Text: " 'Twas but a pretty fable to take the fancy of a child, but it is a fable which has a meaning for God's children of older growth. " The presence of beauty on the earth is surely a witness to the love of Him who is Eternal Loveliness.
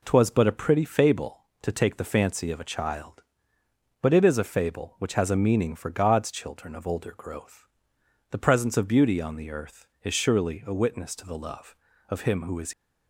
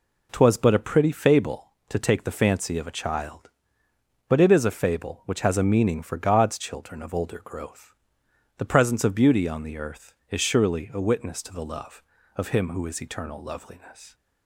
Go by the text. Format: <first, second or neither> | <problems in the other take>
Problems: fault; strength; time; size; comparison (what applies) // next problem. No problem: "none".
second | stops before "Eternal Loveliness"; at 12.7 s